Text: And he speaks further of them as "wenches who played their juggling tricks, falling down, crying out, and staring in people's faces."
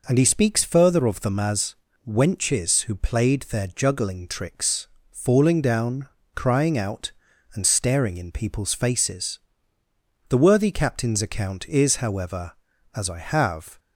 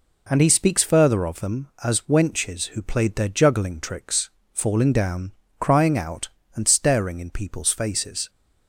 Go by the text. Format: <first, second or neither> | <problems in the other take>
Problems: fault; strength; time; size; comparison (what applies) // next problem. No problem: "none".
second | pauses between "as" and "wenches"; slight; at 1.7 s; 0.32 s long // goes on to say "The worthy Captain's account is however as I have"; strong; from 10.2 s on; 3.5 s long